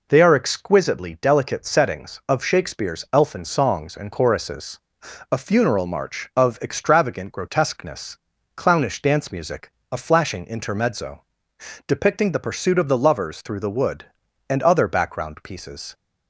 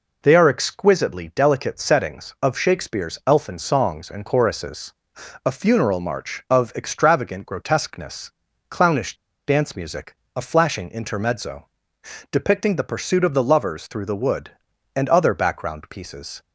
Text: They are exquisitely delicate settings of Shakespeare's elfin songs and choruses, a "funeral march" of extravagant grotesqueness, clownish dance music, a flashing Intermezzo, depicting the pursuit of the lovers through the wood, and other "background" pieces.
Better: first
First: none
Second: pauses between "clownish" and "dance"; slight; at 9.1 s; 0.32 s long

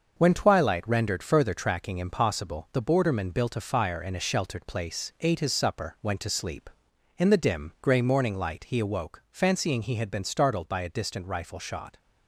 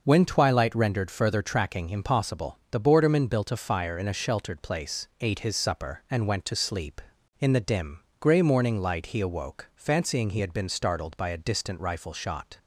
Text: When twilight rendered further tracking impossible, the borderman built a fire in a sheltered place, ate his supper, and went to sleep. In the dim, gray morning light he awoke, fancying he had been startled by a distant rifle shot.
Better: second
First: starts louder than the rest; noticeable; until 1.1 s; 6 dB // skips "and"; at 5.9 s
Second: none

